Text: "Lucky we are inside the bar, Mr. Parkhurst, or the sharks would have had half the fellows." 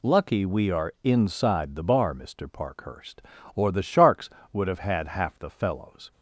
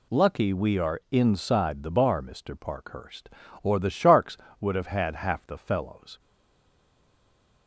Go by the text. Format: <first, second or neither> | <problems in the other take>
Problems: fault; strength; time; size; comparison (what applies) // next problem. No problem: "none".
first | stays silent after the last word; noticeable; from 6.2 s on; 1.4 s long